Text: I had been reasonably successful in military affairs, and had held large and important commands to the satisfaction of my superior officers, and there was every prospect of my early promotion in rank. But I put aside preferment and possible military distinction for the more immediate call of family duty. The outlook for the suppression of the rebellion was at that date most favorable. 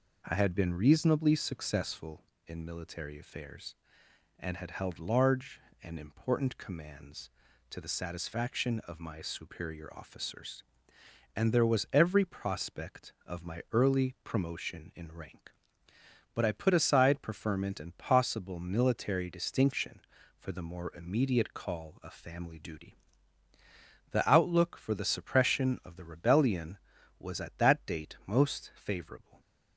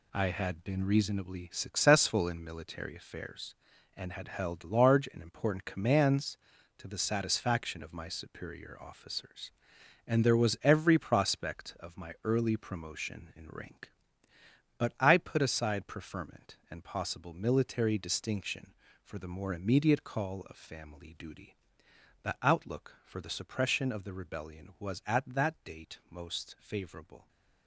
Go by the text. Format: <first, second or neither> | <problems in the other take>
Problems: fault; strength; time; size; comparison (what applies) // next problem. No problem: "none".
first | gets quieter; strong; throughout; 8 dB